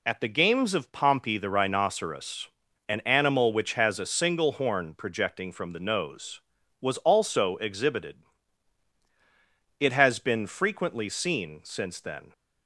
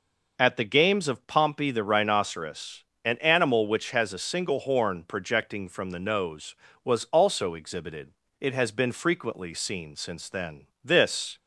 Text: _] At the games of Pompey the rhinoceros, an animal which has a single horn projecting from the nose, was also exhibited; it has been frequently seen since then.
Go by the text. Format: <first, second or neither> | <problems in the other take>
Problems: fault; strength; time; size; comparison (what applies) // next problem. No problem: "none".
first | goes on to say "This"; from 10.8 s on; 0.54 s long